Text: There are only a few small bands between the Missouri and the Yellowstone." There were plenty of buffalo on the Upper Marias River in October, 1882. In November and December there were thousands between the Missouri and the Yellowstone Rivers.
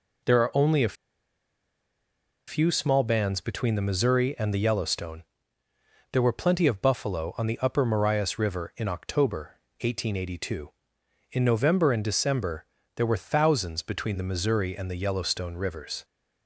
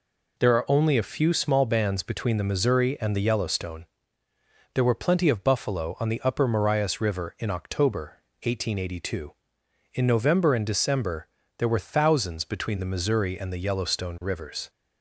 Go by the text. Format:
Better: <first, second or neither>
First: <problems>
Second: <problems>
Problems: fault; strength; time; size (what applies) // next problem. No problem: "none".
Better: second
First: pauses between "a" and "few"; strong; at 0.9 s; 1.5 s long // pauses between "December" and "there"; slight; at 12.6 s; 0.30 s long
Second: pauses between "December" and "there"; slight; at 11.2 s; 0.30 s long